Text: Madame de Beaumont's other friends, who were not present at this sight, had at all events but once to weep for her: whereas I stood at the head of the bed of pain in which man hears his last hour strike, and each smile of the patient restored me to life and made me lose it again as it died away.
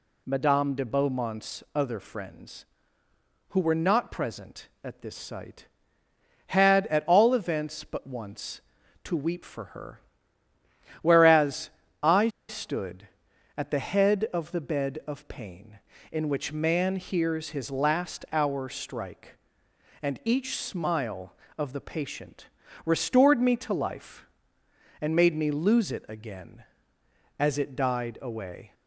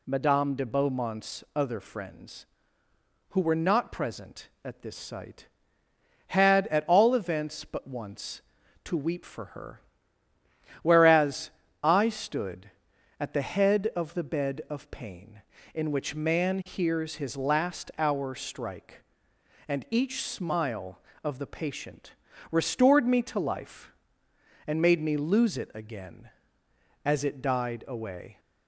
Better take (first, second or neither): second